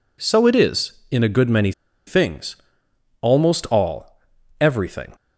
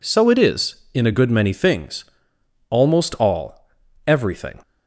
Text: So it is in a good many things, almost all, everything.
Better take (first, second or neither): second